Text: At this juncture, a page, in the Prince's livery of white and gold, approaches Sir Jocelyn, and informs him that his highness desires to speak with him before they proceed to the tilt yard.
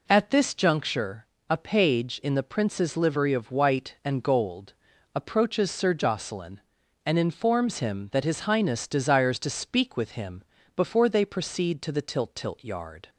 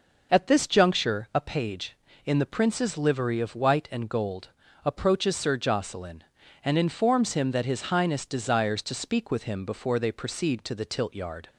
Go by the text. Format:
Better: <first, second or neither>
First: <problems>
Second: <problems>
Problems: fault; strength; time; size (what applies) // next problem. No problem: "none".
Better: second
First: pauses between "him" and "before"; slight; at 10.4 s; 0.32 s long // says "tilt" twice; at 12.3 s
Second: none